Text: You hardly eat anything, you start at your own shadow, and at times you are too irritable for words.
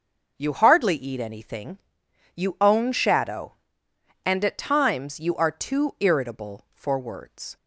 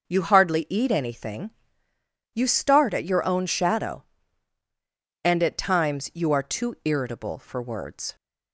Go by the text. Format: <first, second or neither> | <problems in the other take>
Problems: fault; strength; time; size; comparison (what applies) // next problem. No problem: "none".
second | skips "start at your"; at 2.5 s